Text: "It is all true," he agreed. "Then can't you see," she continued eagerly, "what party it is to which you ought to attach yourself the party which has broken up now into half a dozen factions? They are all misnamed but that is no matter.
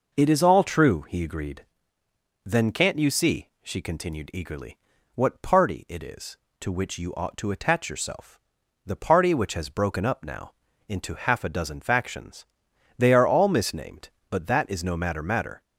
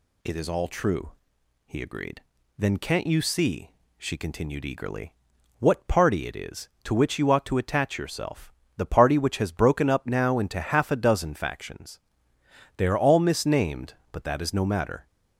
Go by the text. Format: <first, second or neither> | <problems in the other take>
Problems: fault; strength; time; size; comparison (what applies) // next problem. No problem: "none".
second | pauses between "yourself" and "the"; noticeable; at 8.3 s; 0.46 s long; slight in the second // pauses between "now" and "into"; slight; at 10.5 s; 0.34 s long // says "matter" twice; at 15.2 s